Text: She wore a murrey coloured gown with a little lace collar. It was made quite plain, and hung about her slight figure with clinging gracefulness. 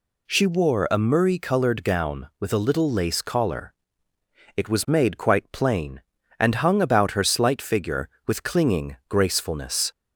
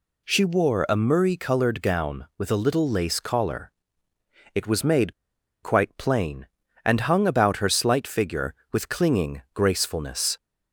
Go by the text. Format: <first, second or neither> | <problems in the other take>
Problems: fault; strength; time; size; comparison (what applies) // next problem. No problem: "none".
first | pauses between "made" and "quite"; noticeable; at 5.1 s; 0.50 s long